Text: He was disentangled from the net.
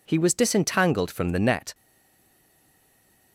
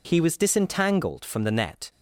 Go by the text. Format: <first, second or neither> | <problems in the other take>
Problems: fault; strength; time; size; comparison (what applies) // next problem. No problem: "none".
second | stays silent after the last word; noticeable; from 1.7 s on; 1.6 s long